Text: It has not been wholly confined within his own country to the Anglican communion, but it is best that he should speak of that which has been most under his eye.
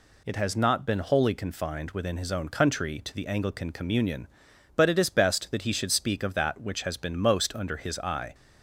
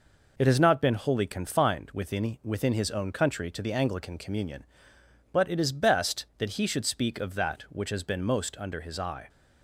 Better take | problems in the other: first | says "within" twice; at 2.4 s

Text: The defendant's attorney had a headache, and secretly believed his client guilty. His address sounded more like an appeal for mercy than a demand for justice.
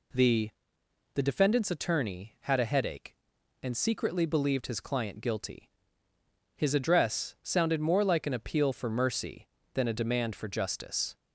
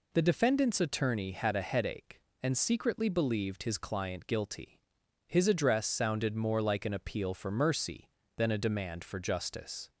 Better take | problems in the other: second | says "The" twice; at 1.1 s

